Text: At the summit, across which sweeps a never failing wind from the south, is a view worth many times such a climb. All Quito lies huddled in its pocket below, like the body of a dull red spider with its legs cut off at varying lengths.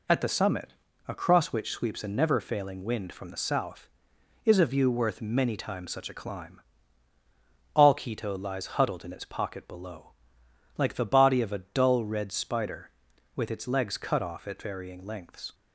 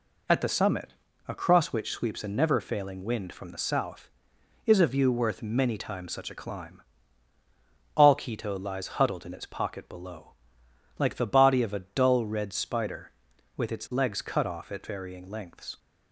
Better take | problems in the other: neither | none

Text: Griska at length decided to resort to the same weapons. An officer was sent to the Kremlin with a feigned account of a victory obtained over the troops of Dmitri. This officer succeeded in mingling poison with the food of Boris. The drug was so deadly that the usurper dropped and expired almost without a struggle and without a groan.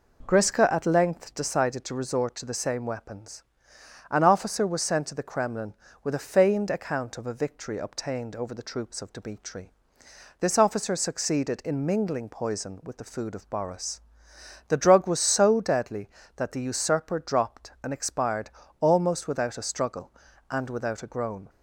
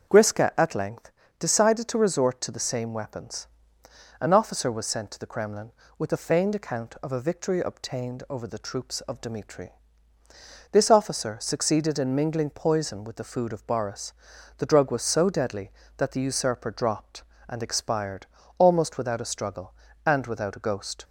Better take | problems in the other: first | starts louder than the rest; until 1.4 s; 7 dB // pauses between "length" and "decided"; slight; at 1.1 s; 0.26 s long // pauses between "expired" and "almost"; slight; at 18.2 s; 0.30 s long; slight in the first // says "ghost" for "groan"; at 20.6 s

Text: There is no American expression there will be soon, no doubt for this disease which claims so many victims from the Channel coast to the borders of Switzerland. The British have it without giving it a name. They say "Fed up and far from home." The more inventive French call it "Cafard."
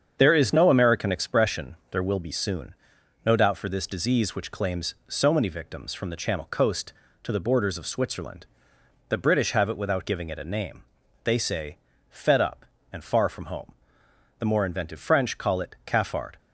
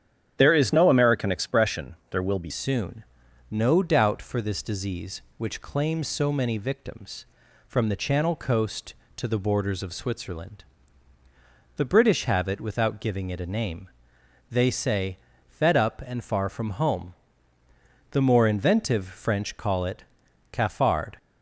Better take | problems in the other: first | starts louder than the rest; strong; until 1.3 s; 9.5 dB; strong in the first // changes voice at "soon"; from 2.4 s on; 18.7 s long // pauses between "say" and "Fed"; at 15.1 s; 0.40 s long; slight in the first // pauses between "it" and "Cafard"; noticeable; at 20.0 s; 0.48 s long

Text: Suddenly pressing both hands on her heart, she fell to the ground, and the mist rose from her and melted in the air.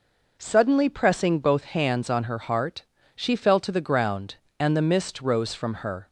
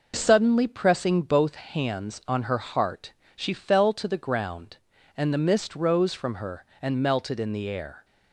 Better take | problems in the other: second | stops before "and melted in the air"; at 6.0 s

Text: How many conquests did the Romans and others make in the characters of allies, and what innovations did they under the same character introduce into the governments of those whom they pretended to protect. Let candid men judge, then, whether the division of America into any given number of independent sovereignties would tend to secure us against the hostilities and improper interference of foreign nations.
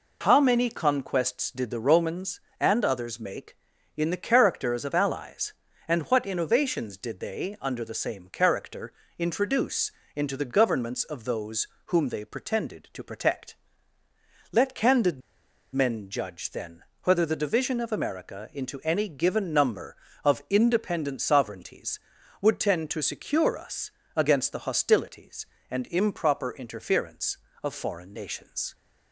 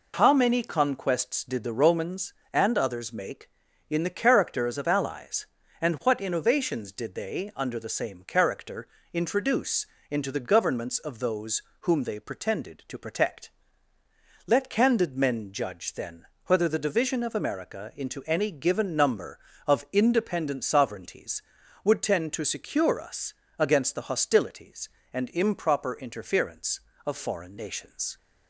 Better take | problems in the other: second | pauses between "character" and "introduce"; slight; at 8.9 s; 0.24 s long; slight in the second // pauses between "introduce" and "into"; slight; at 9.8 s; 0.24 s long; slight in the second // pauses between "those" and "whom"; slight; at 11.6 s; 0.20 s long; slight in the second // pauses between "candid" and "men"; noticeable; at 15.2 s; 0.55 s long // pauses between "us" and "against"; slight; at 23.9 s; 0.24 s long; slight in the second

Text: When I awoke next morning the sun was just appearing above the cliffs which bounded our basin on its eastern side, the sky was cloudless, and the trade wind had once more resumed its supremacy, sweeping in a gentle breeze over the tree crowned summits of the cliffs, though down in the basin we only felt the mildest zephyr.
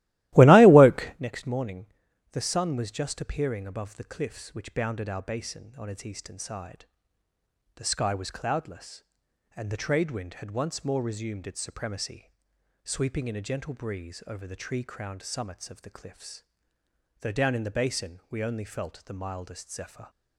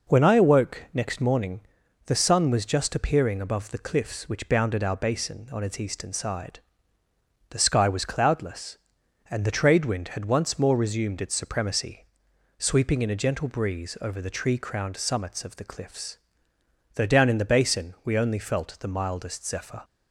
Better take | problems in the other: second | starts louder than the rest; strong; until 1.2 s; 17 dB // pauses between "morning" and "the"; noticeable; at 1.8 s; 0.46 s long; noticeable in the second

